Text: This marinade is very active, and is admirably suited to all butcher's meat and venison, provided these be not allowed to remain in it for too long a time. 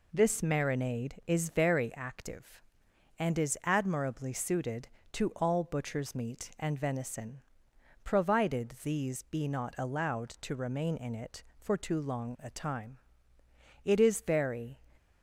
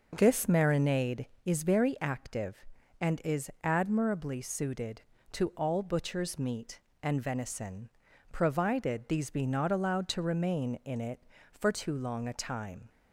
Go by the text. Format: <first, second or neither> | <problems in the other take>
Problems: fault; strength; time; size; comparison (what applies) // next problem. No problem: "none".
second | goes on to say "It is very"; noticeable; from 13.8 s on; 0.94 s long